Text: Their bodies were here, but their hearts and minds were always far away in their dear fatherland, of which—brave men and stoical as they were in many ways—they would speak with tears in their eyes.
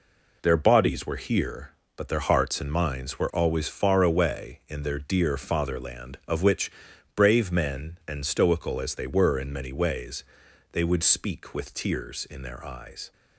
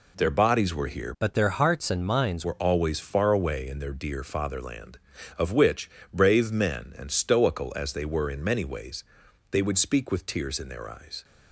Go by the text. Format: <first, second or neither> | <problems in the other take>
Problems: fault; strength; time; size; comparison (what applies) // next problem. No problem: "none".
first | changes voice from "but" to "minds"; from 1.2 to 2.4 s; 1.2 s long